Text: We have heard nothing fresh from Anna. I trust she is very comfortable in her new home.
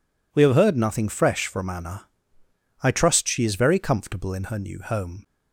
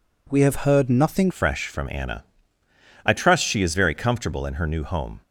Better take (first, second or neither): first